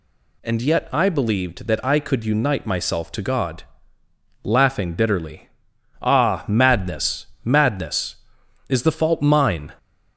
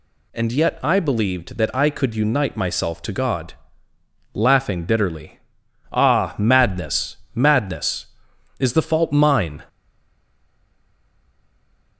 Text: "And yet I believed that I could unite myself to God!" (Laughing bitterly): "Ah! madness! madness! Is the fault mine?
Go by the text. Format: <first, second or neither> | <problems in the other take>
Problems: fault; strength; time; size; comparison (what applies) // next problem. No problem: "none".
first | stays silent after the last word; from 9.6 s on; 2.3 s long